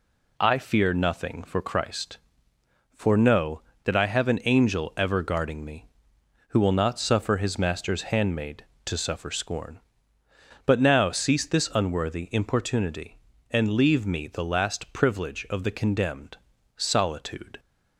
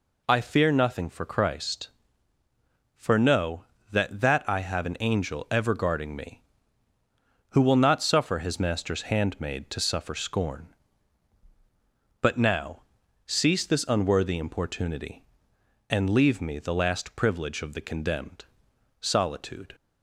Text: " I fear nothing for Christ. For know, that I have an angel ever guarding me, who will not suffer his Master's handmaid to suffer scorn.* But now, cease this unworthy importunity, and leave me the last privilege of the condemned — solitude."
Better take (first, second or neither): first